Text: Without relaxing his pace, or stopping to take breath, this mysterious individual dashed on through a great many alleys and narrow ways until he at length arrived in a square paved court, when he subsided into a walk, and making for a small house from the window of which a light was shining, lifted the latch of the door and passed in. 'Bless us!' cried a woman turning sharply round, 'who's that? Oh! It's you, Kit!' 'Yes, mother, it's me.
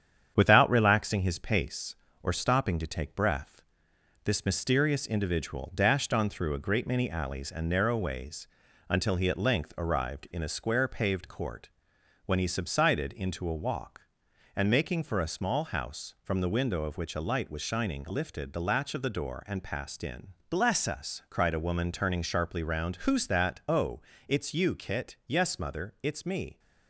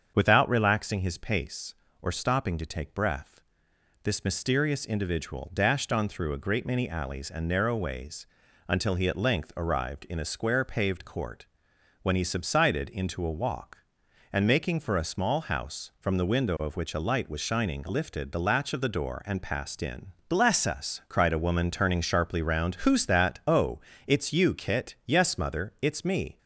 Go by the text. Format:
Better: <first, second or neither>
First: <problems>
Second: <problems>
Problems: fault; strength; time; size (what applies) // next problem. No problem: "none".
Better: second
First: gets quieter; slight; throughout; 3 dB // starts louder than the rest; strong; until 1.3 s; 8.5 dB // pauses between "ways" and "until"; at 8.4 s; 0.40 s long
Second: starts louder than the rest; until 1.1 s; 7 dB // pauses between "ways" and "until"; at 8.2 s; 0.40 s long